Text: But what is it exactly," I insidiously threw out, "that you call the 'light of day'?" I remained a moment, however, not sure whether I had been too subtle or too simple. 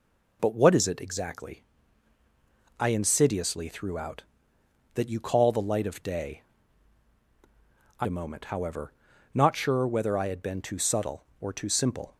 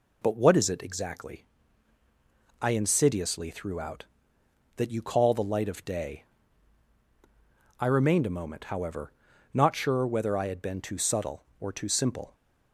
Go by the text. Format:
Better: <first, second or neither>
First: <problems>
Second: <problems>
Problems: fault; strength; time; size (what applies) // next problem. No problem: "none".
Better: second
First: skips "remained"; at 8.0 s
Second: none